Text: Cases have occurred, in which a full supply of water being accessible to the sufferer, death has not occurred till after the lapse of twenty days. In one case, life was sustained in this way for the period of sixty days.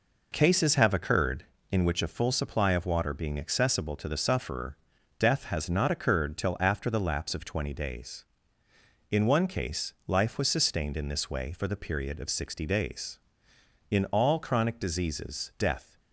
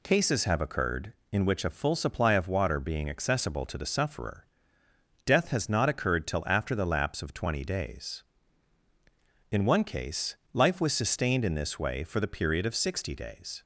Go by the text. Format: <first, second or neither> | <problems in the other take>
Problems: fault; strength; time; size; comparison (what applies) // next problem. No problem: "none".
second | goes on to say "In all chronic diseases death"; strong; from 13.9 s on; 2.0 s long